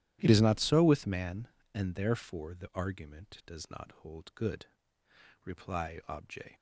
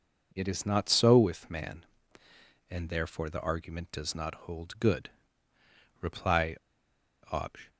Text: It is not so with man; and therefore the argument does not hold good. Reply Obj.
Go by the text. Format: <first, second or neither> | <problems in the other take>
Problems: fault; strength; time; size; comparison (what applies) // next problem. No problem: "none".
first | pauses between "Reply" and "Obj"; noticeable; at 6.5 s; 0.73 s long